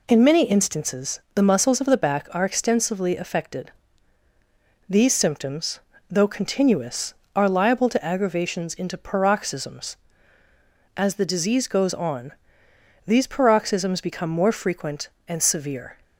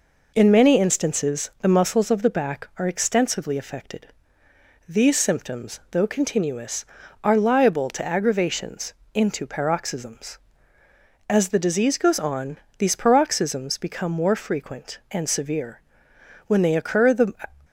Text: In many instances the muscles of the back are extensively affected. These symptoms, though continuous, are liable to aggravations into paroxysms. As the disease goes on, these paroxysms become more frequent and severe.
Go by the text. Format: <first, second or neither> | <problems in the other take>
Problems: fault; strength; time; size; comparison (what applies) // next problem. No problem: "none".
first | pauses between "aggravations" and "into"; slight; at 8.9 s; 0.22 s long // goes on to say "When they occur the"; noticeable; from 16.4 s on; 0.86 s long